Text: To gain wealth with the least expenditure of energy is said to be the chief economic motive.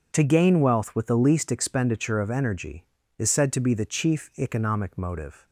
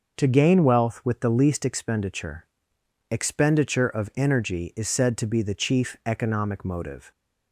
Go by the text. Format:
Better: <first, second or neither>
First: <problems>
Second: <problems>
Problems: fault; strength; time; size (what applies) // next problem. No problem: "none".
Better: first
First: none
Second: starts louder than the rest; noticeable; until 1.2 s; 6 dB // says "expenditure" twice; at 3.1 s